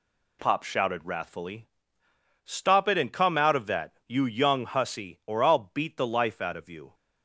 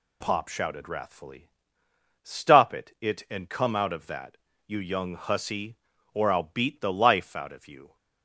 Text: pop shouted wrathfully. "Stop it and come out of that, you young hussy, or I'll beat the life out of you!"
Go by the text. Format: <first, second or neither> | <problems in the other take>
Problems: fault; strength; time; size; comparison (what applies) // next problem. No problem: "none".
first | says "it" twice; at 3.0 s